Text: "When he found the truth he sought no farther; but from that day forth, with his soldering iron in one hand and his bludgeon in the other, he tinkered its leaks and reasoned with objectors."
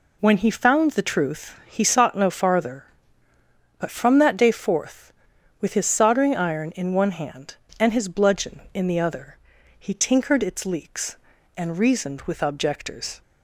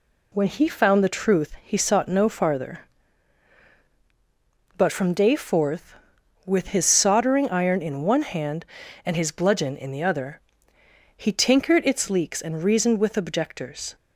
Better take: first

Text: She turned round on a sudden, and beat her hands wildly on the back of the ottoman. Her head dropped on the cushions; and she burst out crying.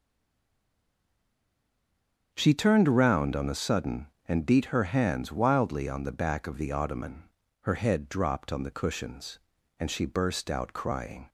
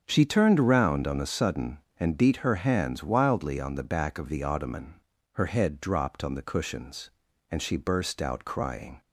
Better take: second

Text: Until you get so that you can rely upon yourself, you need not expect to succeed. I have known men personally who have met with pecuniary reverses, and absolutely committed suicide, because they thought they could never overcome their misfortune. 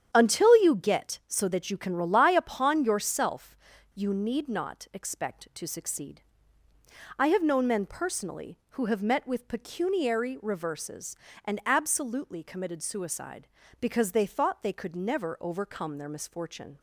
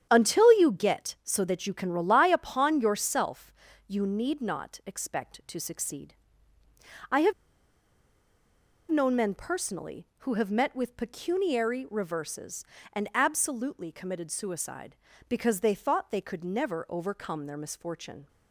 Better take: first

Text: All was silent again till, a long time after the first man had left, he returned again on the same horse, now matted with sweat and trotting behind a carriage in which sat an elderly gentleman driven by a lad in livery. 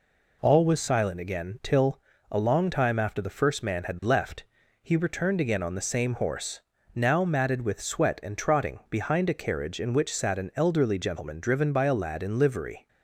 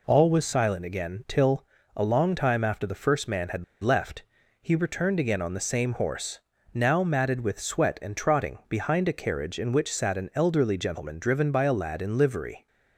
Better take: first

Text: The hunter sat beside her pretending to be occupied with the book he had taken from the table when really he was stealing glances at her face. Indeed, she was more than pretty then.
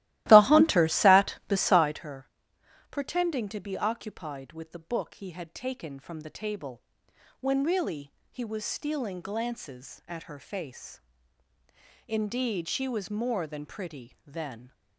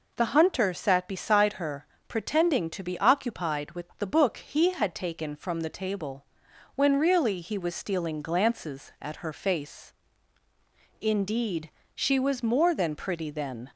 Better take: second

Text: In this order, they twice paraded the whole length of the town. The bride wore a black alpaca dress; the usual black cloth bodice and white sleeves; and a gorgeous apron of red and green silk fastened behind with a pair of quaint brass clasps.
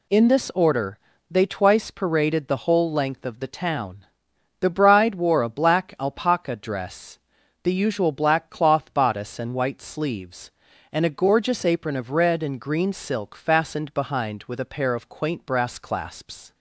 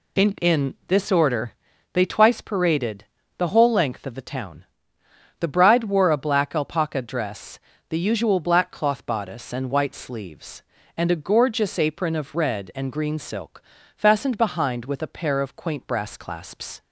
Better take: first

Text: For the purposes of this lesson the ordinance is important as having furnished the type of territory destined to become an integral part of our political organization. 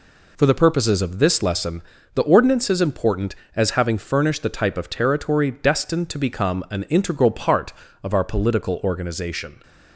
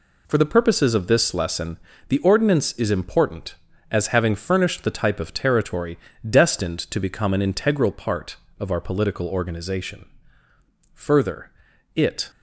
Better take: first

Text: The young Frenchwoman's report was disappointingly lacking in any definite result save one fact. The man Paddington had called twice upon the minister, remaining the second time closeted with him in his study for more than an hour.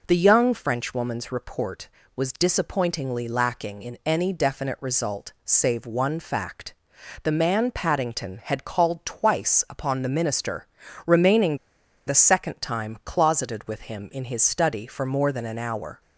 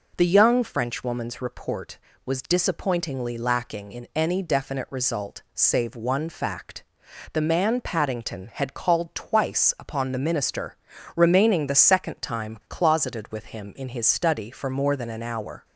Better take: second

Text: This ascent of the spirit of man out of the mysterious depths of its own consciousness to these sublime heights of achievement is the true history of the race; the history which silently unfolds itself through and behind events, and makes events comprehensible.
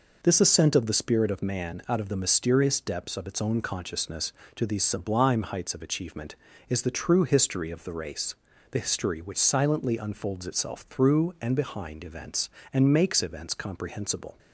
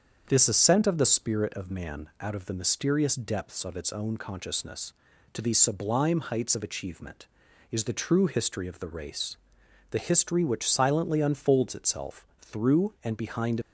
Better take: first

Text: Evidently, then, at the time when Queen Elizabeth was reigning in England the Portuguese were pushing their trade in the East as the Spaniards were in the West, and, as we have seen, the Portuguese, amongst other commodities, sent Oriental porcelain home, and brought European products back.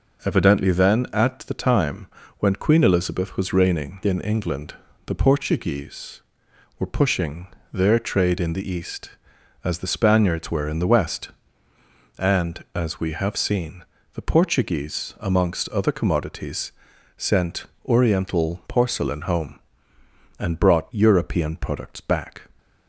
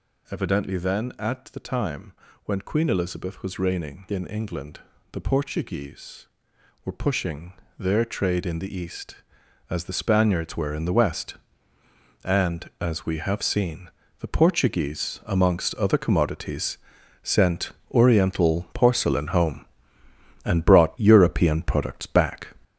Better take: first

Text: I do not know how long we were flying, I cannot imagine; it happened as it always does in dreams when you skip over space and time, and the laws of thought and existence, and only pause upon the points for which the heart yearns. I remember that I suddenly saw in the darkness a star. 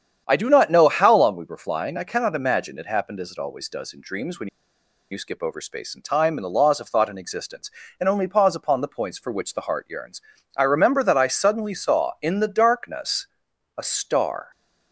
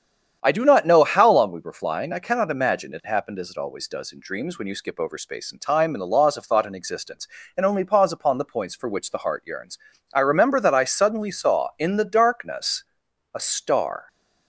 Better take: second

